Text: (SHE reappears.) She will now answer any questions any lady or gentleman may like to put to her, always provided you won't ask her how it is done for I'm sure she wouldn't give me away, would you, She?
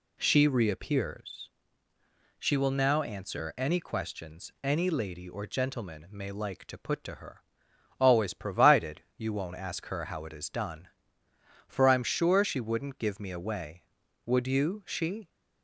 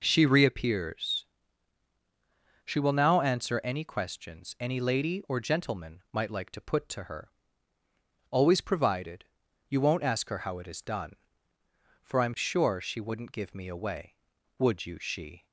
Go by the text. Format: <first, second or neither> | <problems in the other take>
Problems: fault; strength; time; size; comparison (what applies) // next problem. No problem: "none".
first | says "might" for "may"; at 6.1 s // pauses between "provided" and "you"; noticeable; at 9.2 s; 0.46 s long